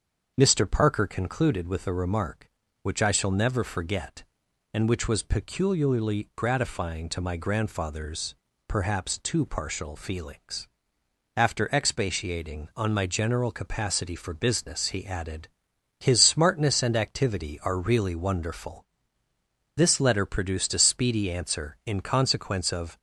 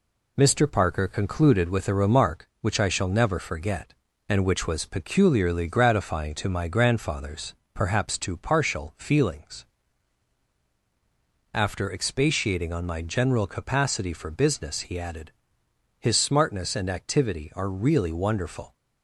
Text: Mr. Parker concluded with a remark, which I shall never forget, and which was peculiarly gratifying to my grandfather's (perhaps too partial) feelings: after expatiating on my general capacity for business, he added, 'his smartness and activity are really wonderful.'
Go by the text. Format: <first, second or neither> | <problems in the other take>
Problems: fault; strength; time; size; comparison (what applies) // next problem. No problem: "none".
second | starts louder than the rest; until 1.3 s; 7 dB // goes on to say "This letter produced a speedy answer in consequence of"; strong; from 19.7 s on; 3.2 s long